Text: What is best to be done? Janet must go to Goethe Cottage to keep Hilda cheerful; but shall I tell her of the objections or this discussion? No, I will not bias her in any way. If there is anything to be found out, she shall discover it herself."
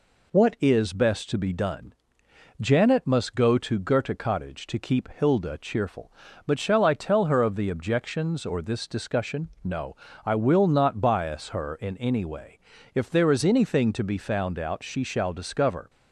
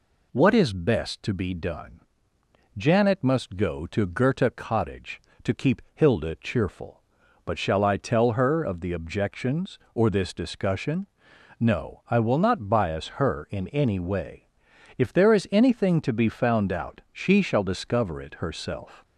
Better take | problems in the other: second | stops before "it herself"; at 15.8 s

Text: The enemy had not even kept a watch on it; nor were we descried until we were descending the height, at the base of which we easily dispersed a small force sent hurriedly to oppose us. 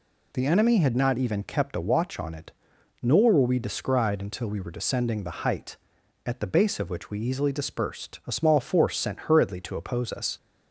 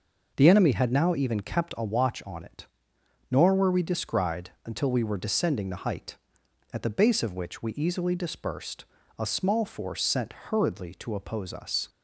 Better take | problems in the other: first | says "now" for "not"; at 0.9 s // pauses between "descried" and "until"; slight; at 4.4 s; 0.16 s long // pauses between "dispersed" and "a"; slight; at 8.8 s; 0.34 s long // pauses between "sent" and "hurriedly"; slight; at 10.3 s; 0.20 s long

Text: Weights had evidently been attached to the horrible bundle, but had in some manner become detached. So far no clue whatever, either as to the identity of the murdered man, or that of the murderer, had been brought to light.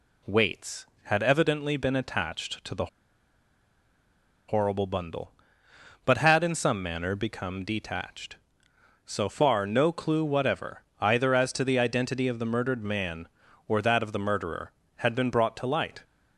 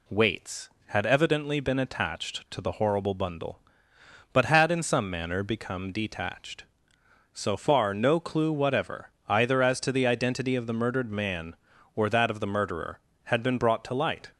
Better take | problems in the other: second | pauses between "the" and "horrible"; strong; at 2.8 s; 1.6 s long

